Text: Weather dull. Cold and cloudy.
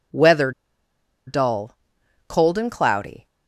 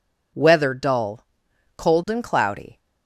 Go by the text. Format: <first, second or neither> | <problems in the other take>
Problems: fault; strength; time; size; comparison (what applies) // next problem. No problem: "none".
second | pauses between "Weather" and "dull"; noticeable; at 0.5 s; 0.76 s long